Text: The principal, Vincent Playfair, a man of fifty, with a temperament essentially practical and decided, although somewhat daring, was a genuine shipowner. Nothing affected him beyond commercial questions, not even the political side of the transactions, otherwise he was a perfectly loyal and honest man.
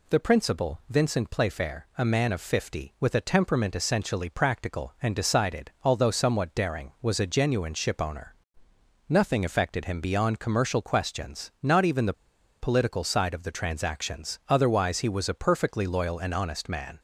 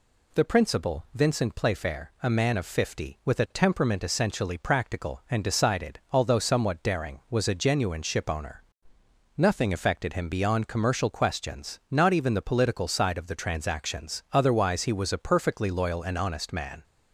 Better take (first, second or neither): second